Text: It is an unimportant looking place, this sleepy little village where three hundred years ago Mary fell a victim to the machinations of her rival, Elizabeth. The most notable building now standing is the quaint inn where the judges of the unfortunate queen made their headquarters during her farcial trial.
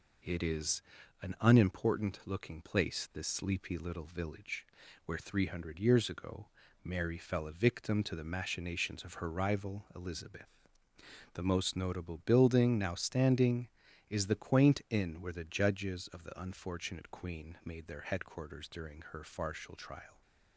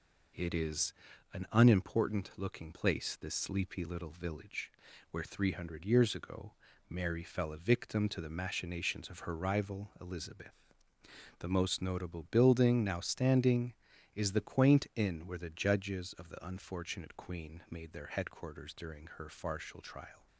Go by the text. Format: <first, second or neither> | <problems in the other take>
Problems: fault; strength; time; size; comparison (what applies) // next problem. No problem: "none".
neither | pauses between "is" and "an"; the same in both // pauses between "village" and "where"; the same in both // pauses between "ago" and "Mary"; slight; the same in both